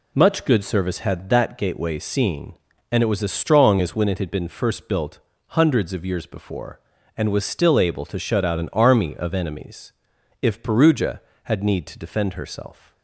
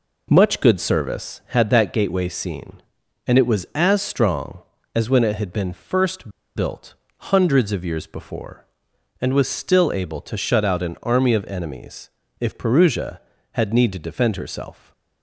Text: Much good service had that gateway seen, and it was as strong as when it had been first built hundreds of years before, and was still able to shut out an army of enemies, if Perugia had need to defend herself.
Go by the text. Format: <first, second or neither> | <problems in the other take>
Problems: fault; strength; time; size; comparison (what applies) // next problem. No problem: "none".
first | pauses between "first" and "built"; slight; at 6.2 s; 0.26 s long // pauses between "built" and "hundreds"; slight; at 6.9 s; 0.24 s long; slight in the first